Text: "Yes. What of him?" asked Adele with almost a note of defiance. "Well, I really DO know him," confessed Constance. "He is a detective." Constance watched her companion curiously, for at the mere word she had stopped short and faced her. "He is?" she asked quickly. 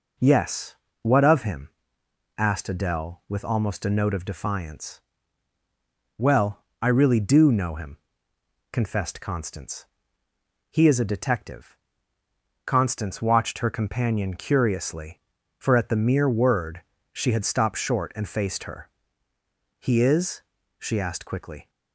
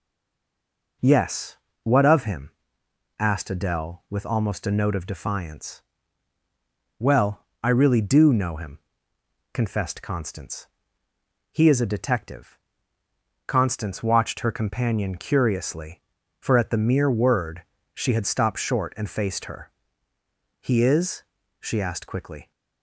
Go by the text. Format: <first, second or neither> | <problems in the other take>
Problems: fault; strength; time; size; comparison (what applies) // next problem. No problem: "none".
first | stays silent before the first word; until 1.0 s; 1.0 s long // pauses between "word" and "she"; slight; at 17.6 s; 0.32 s long; slight in the first